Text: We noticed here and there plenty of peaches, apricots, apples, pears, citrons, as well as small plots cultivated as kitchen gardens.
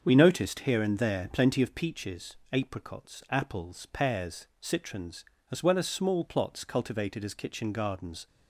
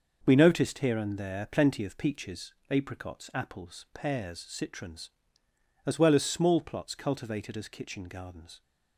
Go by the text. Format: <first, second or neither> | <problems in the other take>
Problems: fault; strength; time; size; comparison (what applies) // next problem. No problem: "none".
neither | starts louder than the rest; the same in both